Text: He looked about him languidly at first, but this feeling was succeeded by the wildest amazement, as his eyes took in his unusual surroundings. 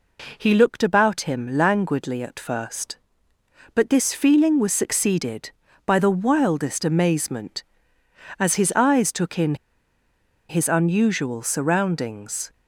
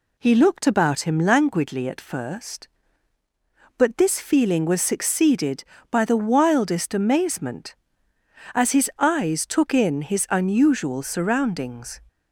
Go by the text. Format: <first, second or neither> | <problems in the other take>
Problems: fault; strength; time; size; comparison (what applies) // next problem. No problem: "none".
second | pauses between "in" and "his"; noticeable; at 9.5 s; 0.94 s long